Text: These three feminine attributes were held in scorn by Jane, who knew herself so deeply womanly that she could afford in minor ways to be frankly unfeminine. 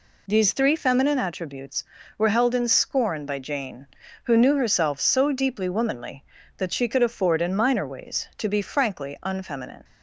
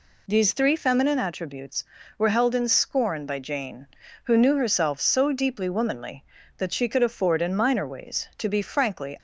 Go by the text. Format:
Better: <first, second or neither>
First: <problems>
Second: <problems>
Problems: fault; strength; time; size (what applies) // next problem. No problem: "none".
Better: first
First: none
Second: stops before "unfeminine"; at 9.1 s